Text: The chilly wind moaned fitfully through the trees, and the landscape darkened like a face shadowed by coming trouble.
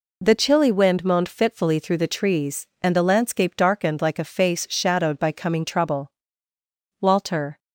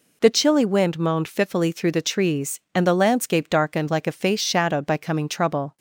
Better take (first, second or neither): second